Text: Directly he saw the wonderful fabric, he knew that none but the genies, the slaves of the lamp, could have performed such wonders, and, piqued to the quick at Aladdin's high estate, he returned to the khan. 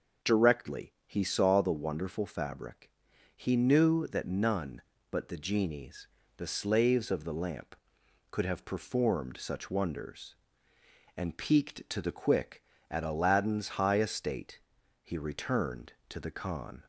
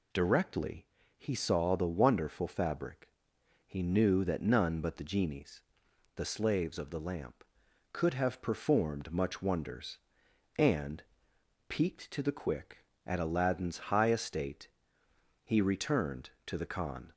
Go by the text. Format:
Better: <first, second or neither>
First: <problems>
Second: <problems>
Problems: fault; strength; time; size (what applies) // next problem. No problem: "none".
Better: first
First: none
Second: pauses between "Directly" and "he"; slight; at 0.8 s; 0.32 s long // says "much" for "such"; at 9.1 s